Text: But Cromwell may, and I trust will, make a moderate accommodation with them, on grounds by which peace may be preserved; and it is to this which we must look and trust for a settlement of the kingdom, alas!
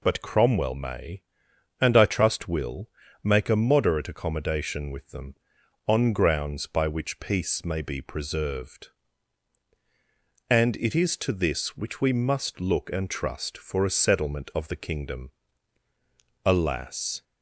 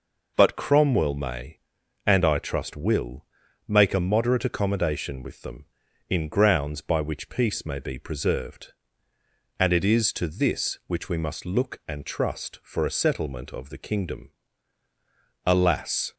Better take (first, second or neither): first